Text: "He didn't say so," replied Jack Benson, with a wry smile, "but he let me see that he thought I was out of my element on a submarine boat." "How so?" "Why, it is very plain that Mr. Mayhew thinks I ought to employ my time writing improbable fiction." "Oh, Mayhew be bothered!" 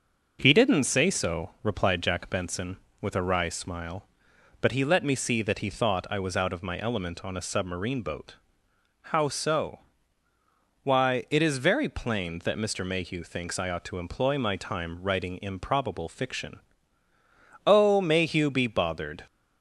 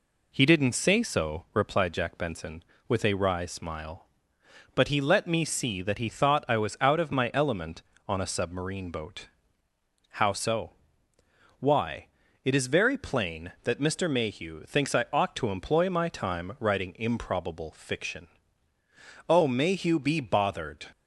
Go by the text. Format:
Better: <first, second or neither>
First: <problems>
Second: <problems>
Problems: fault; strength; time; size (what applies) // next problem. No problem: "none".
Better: neither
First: none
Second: none